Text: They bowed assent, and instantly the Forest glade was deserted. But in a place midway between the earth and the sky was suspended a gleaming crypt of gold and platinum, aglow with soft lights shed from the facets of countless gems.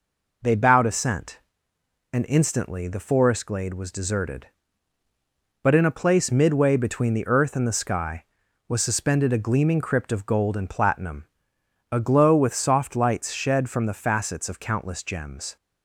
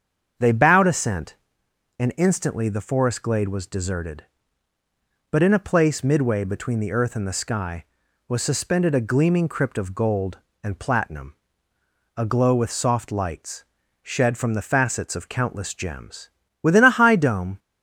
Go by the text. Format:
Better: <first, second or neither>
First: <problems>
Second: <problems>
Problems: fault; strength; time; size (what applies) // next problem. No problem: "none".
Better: first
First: none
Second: starts louder than the rest; strong; until 2.0 s; 7.5 dB // pauses between "lights" and "shed"; at 13.6 s; 0.40 s long // goes on to say "Within a high dome"; noticeable; from 16.6 s on; 0.98 s long